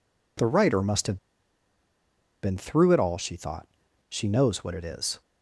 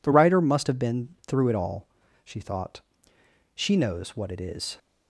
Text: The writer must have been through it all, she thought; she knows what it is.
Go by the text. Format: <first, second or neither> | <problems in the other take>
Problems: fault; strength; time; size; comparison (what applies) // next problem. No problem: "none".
second | pauses between "have" and "been"; strong; at 1.1 s; 1.2 s long